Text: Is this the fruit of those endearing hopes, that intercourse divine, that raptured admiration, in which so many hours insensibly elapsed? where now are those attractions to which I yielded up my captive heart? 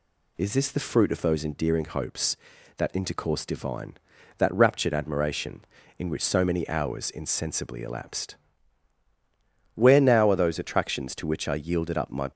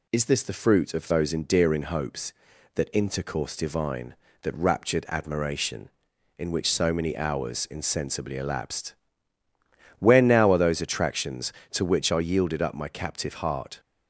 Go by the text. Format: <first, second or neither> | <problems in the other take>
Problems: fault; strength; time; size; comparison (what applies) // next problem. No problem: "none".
second | stops before "captive heart"; at 12.3 s